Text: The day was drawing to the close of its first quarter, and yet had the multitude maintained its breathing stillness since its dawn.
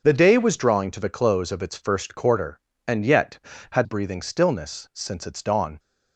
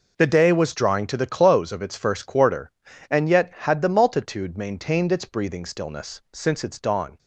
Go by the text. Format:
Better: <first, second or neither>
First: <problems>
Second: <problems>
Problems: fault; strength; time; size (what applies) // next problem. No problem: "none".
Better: second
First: starts louder than the rest; until 1.0 s; 6 dB // skips "the multitude maintained its"; at 3.8 s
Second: none